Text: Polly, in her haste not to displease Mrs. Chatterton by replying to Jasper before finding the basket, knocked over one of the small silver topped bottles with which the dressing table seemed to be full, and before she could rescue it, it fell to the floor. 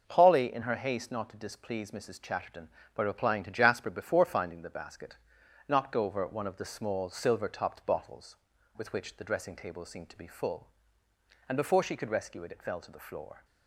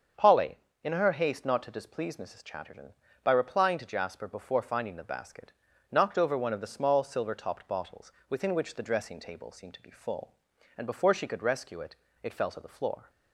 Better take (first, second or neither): first